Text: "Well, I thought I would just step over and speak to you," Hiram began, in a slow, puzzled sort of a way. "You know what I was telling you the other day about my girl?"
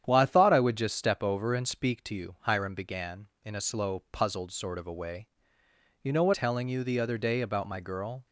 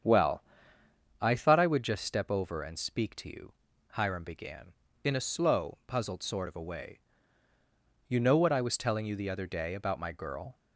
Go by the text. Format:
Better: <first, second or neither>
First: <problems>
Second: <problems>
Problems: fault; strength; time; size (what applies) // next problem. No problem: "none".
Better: second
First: starts louder than the rest; strong; until 1.0 s; 9.5 dB // skips "I was"; at 6.3 s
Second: starts louder than the rest; strong; until 1.8 s; 8 dB